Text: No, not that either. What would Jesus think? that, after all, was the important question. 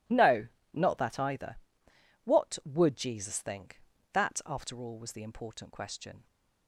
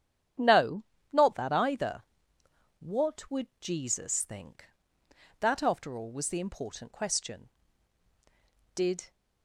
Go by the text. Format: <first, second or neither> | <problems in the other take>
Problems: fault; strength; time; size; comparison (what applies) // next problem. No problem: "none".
first | starts louder than the rest; strong; until 1.6 s; 9 dB // goes on to say "Did"; slight; from 8.7 s on; 0.36 s long